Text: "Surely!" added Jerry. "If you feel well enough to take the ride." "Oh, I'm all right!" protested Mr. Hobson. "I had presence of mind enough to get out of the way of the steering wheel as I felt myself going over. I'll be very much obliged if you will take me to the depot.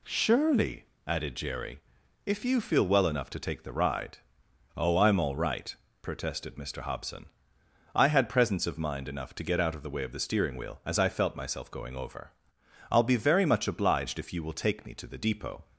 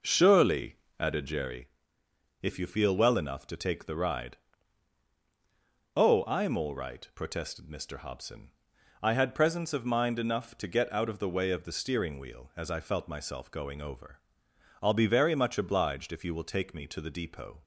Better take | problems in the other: first | starts louder than the rest; noticeable; until 1.6 s; 5 dB

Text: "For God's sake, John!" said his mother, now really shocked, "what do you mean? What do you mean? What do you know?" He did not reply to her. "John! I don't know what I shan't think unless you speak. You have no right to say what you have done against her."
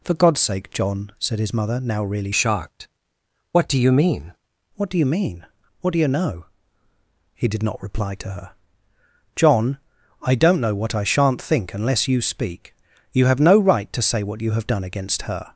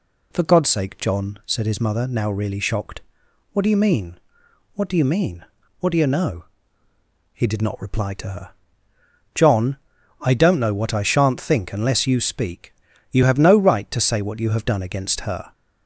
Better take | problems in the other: second | changes voice from "shocked" to "mean"; from 2.3 to 4.3 s; 2.0 s long

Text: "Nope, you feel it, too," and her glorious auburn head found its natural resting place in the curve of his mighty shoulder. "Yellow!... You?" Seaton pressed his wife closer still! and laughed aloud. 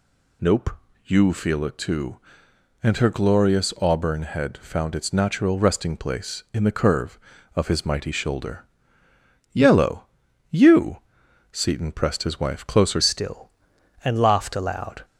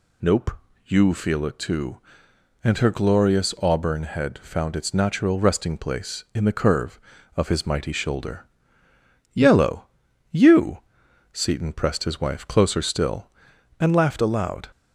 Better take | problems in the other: second | changes voice at "still"; from 13.0 s on; 2.0 s long

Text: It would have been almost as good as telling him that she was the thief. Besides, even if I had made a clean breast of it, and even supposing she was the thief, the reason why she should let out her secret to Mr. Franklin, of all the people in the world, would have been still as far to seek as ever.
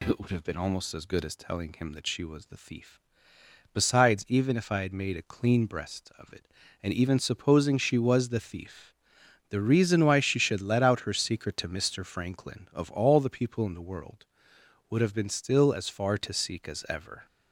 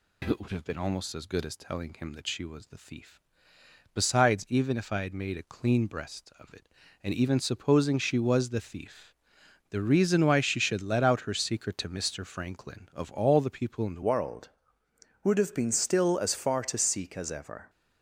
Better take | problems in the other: first | changes voice at "world"; from 14.0 s on; 3.6 s long

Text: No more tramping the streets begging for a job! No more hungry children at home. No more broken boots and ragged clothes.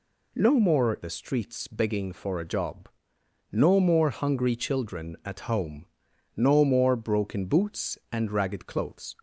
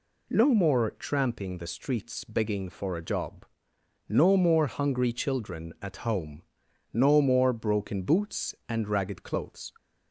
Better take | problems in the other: second | skips "tramping"; at 0.9 s

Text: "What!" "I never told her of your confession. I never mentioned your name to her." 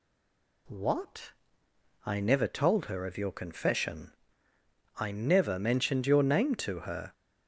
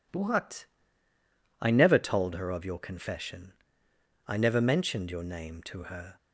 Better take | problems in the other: second | stays silent before the first word; slight; until 0.6 s; 0.6 s long

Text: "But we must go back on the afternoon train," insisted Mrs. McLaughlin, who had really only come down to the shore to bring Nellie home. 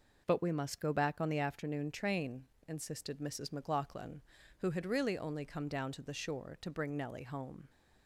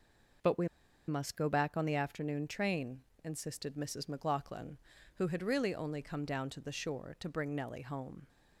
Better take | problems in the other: first | pauses between "we" and "must"; at 0.6 s; 0.40 s long

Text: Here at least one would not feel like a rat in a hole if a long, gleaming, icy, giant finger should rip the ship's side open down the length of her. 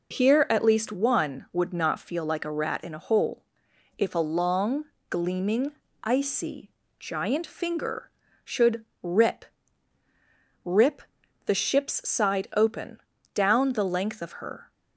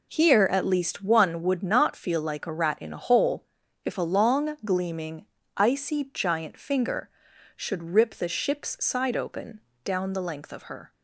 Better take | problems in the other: second | pauses between "hole" and "if"; noticeable; at 3.4 s; 0.52 s long; also in the second // pauses between "should" and "rip"; slight; at 8.8 s; 0.18 s long // says "rip" twice; at 10.6 s // pauses between "open" and "down"; slight; at 12.9 s; 0.36 s long; slight in the second

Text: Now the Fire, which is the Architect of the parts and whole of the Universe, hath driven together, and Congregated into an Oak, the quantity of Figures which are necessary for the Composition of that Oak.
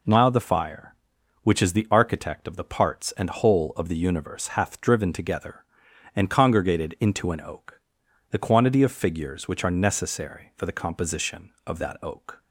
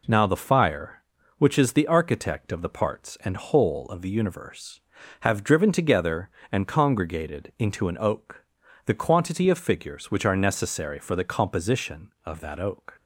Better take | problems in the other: first | says "have" for "hath"; at 5.2 s

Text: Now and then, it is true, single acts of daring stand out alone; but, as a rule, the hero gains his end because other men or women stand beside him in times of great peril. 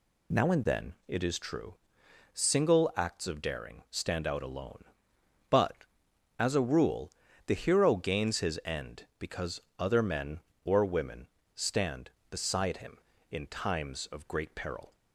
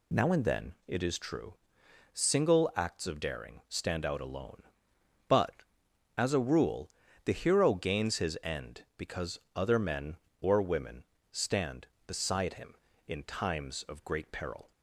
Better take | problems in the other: neither | pauses between "because" and "other"; slight; the same in both // pauses between "women" and "stand"; slight; the same in both

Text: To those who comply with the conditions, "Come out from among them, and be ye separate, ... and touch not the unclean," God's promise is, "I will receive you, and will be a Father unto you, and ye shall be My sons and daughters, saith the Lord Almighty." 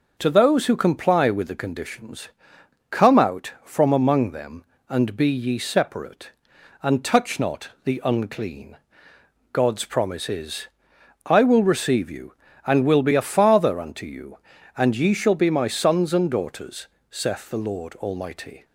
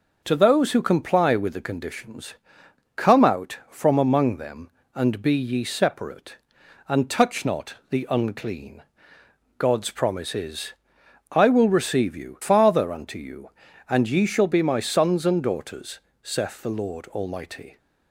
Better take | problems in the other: first | pauses between "not" and "the"; slight; at 7.7 s; 0.16 s long; slight in the first // skips "and will be a"; at 12.4 s

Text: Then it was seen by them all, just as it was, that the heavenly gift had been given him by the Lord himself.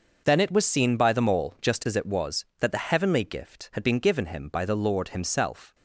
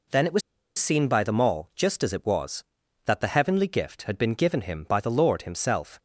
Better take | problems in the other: first | pauses between "was" and "seen"; at 0.4 s; 0.37 s long

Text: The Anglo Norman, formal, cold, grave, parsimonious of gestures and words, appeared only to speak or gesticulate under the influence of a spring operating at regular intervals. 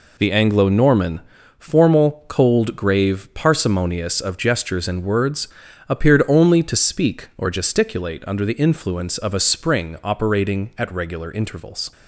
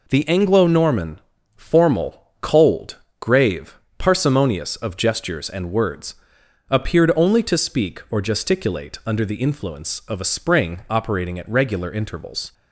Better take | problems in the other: neither | none

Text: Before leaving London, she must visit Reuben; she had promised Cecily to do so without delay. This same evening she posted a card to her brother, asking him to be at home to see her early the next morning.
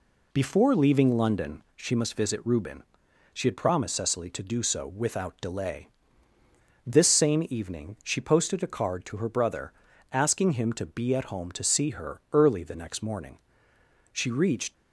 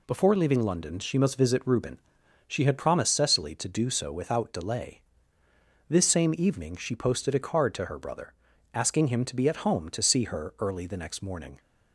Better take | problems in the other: second | goes on to say "She reached"; from 14.1 s on; 0.60 s long

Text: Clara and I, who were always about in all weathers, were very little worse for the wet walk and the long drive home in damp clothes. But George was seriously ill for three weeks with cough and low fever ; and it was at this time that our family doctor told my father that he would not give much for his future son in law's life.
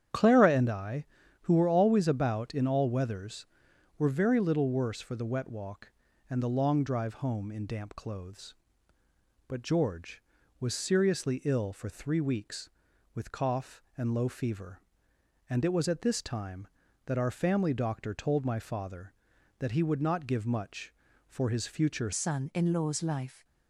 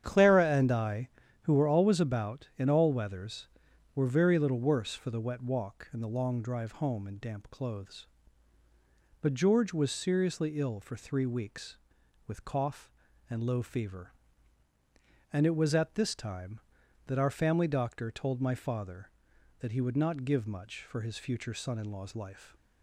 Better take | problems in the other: second | starts louder than the rest; strong; until 1.5 s; 9 dB; strong in the second // changes voice at "son"; from 22.1 s on; 1.3 s long

